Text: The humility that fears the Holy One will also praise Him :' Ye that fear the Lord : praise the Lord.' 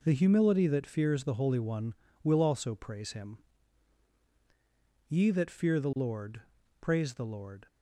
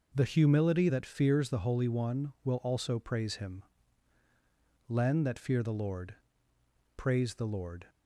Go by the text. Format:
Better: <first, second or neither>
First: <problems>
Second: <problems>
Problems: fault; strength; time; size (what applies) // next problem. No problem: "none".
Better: first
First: none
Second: starts louder than the rest; noticeable; until 1.1 s; 6 dB // says "Len" for "Ye"; at 4.8 s